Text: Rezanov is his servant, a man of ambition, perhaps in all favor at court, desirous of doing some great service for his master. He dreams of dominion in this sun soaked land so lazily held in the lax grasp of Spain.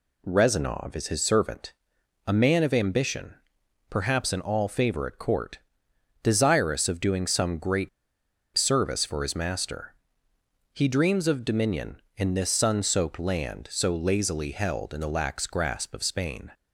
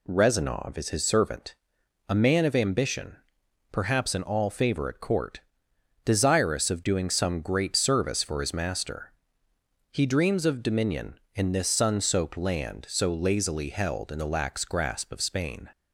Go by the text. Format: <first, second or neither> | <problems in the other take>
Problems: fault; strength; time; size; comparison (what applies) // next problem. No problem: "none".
second | pauses between "great" and "service"; noticeable; at 7.8 s; 0.67 s long